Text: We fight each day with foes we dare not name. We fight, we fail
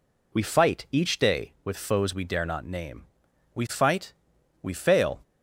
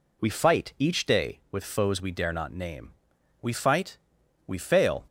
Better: neither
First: none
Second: none

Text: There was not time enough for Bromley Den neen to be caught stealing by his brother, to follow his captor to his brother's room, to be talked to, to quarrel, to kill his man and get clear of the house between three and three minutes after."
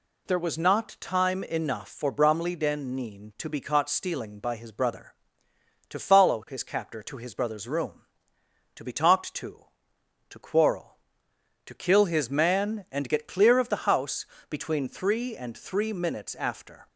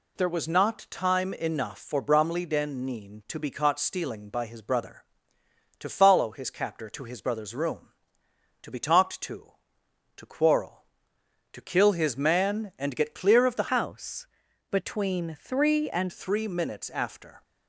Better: first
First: pauses between "house" and "between"; slight; at 14.2 s; 0.24 s long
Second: changes voice from "house" to "and"; from 13.7 to 16.1 s; 2.4 s long // pauses between "house" and "between"; at 14.2 s; 0.44 s long

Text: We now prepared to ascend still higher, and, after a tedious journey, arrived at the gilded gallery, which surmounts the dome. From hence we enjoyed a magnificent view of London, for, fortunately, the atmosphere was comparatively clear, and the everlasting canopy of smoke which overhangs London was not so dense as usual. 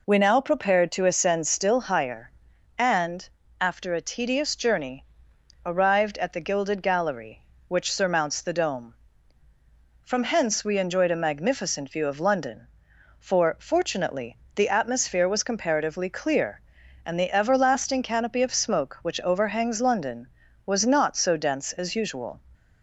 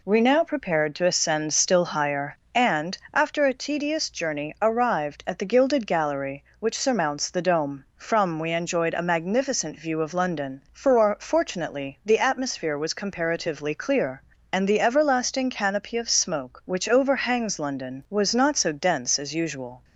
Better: first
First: none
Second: skips "hence"; at 8.3 s

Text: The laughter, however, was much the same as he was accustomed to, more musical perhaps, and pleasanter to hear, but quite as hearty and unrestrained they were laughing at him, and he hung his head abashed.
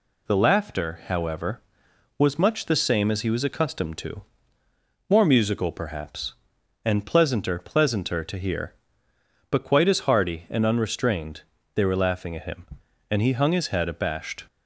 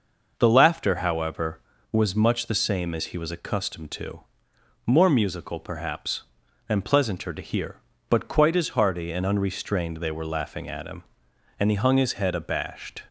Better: second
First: says "pleasanter" twice; at 7.5 s // pauses between "unrestrained" and "they"; slight; at 11.4 s; 0.32 s long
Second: none

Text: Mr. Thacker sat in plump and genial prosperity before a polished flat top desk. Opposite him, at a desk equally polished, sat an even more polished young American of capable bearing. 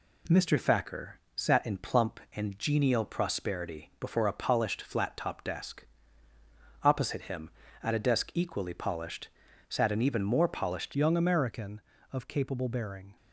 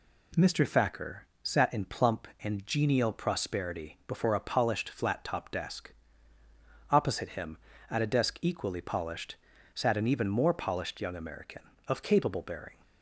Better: second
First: pauses between "Thacker" and "sat"; slight; at 1.1 s; 0.18 s long // changes voice at "young"; from 10.9 s on; 2.2 s long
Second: pauses between "Thacker" and "sat"; slight; at 1.2 s; 0.18 s long

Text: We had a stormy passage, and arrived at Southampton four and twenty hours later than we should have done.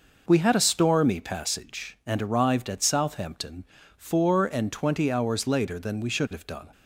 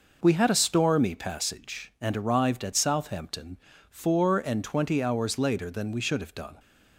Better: neither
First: pauses between "Southampton" and "four"; slight; at 3.6 s; 0.32 s long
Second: pauses between "Southampton" and "four"; slight; at 3.5 s; 0.32 s long

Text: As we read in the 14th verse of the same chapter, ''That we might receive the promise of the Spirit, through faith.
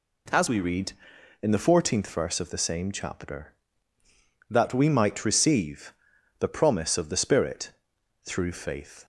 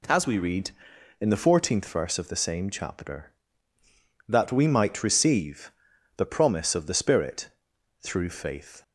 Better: neither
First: pauses between "receive" and "the"; noticeable; at 5.9 s; 0.46 s long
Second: pauses between "receive" and "the"; at 5.7 s; 0.45 s long

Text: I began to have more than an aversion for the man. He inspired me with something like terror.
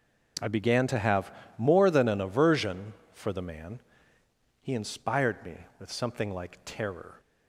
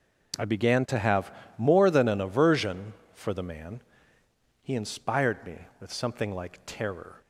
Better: neither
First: pauses between "have" and "more"; slight; at 1.3 s; 0.26 s long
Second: pauses between "have" and "more"; slight; at 1.3 s; 0.26 s long

